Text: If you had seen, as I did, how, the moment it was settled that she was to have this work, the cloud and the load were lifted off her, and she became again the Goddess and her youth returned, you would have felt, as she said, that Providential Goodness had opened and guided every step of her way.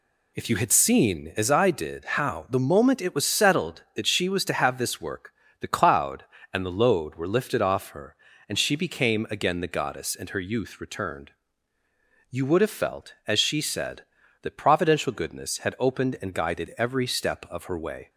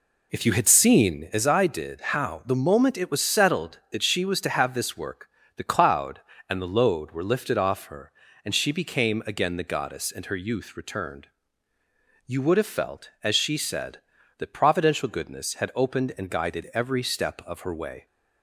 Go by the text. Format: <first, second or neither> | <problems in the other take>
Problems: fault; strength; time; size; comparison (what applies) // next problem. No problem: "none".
first | starts louder than the rest; slight; until 1.3 s; 3 dB